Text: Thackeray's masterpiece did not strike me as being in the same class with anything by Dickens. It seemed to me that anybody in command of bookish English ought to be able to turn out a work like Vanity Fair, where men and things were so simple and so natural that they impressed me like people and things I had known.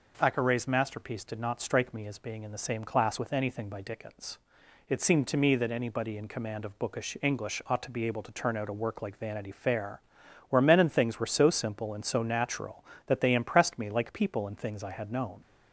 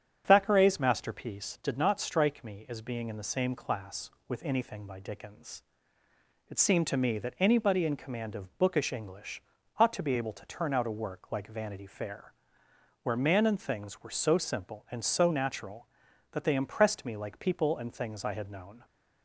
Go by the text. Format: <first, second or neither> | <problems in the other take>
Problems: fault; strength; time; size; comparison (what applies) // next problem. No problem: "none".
first | starts louder than the rest; strong; until 1.2 s; 8.5 dB // pauses between "English" and "ought"; at 9.3 s; 0.38 s long // says "man" for "men"; at 13.1 s